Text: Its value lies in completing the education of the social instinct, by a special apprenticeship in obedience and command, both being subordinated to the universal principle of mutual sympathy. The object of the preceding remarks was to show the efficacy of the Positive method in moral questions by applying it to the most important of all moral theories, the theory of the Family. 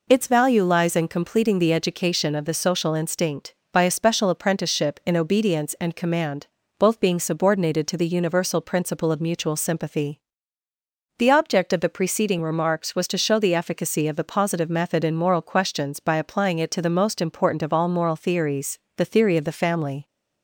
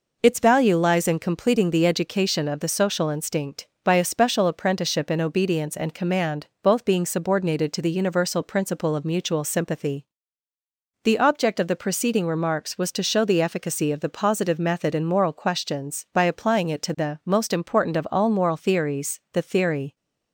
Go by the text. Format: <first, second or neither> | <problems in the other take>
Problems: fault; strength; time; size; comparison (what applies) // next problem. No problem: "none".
first | stops before "of the Family"; at 19.9 s